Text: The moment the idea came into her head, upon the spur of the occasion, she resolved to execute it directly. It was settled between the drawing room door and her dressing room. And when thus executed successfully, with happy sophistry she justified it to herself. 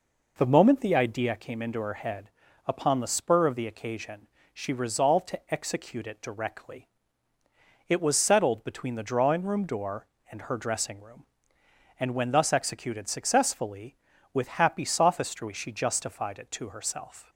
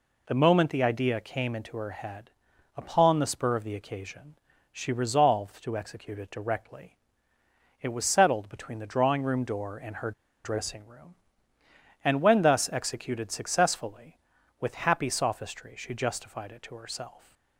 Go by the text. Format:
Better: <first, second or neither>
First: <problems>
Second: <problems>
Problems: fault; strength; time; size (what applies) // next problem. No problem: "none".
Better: first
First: none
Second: pauses between "her" and "dressing"; slight; at 10.1 s; 0.33 s long